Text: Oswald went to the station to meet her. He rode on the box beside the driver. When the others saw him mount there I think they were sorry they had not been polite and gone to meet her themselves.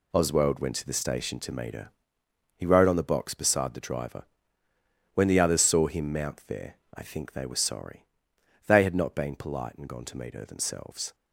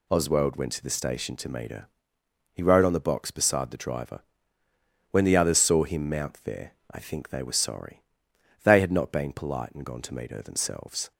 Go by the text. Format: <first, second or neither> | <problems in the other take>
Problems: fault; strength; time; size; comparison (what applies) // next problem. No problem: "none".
second | gets quieter; strong; throughout; 8.5 dB // pauses between "there" and "I"; slight; at 6.7 s; 0.18 s long; slight in the second // pauses between "sorry" and "they"; noticeable; at 8.0 s; 0.64 s long; noticeable in the second